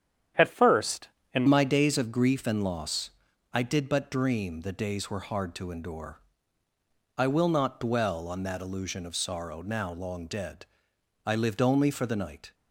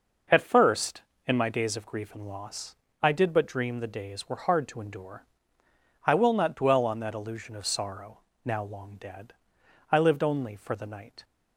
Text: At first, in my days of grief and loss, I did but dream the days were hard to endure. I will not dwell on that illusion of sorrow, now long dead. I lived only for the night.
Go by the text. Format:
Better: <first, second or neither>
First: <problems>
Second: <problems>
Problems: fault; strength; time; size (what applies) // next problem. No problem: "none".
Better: second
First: starts louder than the rest; strong; until 1.6 s; 9.5 dB // changes voice at "my"; from 1.4 s on; 11.1 s long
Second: none